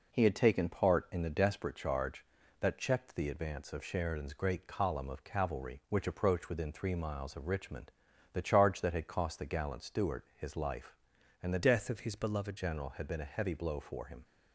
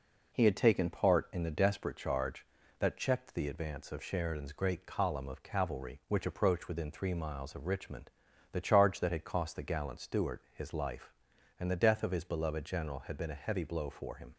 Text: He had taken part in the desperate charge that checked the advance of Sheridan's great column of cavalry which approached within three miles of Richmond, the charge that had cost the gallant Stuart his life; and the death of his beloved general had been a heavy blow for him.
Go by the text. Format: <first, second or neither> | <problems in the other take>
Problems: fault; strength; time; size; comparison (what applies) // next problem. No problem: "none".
second | changes voice from "death" to "beloved"; from 11.6 to 12.5 s; 0.9 s long